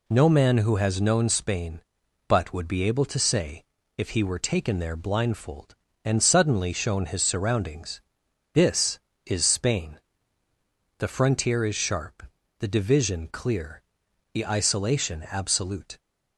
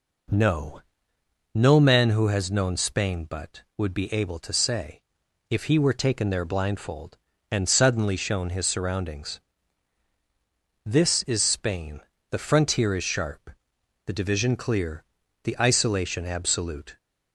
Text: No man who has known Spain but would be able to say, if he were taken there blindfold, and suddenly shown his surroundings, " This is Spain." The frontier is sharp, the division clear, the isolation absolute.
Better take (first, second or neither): first